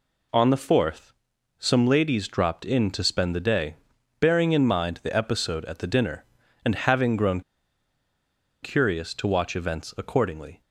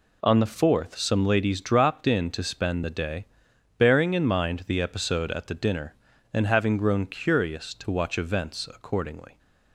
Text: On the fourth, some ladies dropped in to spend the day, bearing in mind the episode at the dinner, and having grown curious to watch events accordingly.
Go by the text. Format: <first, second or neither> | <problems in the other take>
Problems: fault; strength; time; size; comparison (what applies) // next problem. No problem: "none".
second | pauses between "grown" and "curious"; at 7.4 s; 1.2 s long